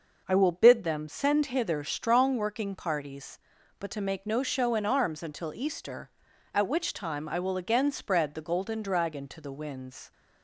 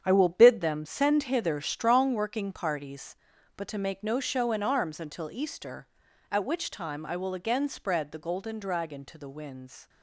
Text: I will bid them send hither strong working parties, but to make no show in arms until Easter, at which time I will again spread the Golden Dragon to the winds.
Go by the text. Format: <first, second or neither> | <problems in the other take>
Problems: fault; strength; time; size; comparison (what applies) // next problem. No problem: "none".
first | gets quieter; strong; throughout; 10 dB